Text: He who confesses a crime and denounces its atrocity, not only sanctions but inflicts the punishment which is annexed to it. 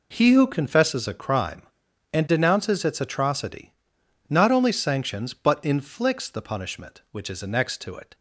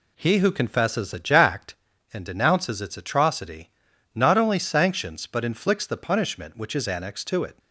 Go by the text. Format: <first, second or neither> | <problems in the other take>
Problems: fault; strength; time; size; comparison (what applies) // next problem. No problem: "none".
first | says "jacked" for "crime"; at 1.1 s